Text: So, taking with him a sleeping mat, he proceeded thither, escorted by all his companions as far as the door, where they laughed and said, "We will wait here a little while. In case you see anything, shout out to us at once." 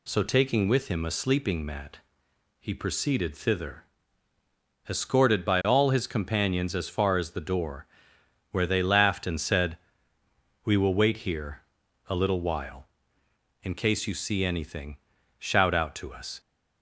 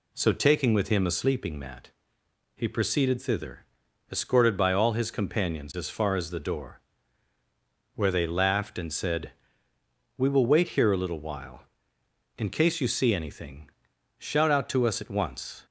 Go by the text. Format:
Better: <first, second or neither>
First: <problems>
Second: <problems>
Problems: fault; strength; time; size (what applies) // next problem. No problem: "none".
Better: second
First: pauses between "here" and "a"; noticeable; at 11.6 s; 0.46 s long // stops before "at once"; at 16.3 s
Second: none